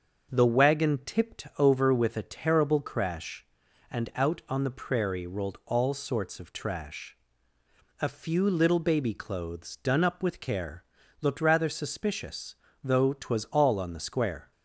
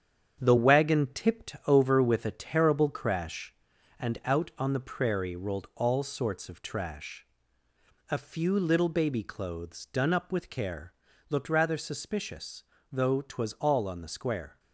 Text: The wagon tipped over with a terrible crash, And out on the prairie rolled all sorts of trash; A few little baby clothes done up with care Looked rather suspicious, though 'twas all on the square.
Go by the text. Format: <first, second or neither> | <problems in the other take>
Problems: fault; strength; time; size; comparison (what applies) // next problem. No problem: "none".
first | gets quieter; strong; throughout; 7.5 dB // starts louder than the rest; strong; until 1.4 s; 8 dB; also in the first // pauses between "care" and "Looked"; at 10.9 s; 0.36 s long; also in the first